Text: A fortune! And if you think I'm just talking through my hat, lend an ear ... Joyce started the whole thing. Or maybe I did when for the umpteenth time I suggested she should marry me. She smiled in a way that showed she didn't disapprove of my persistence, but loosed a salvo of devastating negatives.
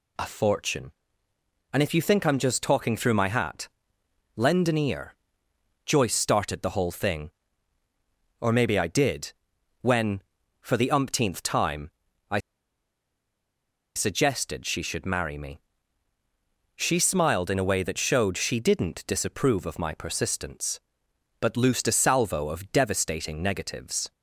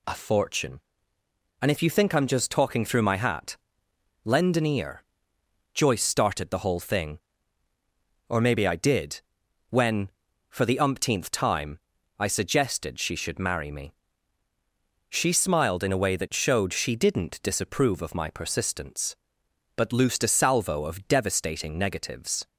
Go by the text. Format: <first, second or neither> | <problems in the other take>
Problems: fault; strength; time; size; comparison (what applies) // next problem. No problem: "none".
second | pauses between "did" and "when"; noticeable; at 9.3 s; 0.48 s long; noticeable in the second // pauses between "time" and "I"; at 11.8 s; 0.40 s long; also in the second // pauses between "I" and "suggested"; strong; at 12.3 s; 1.5 s long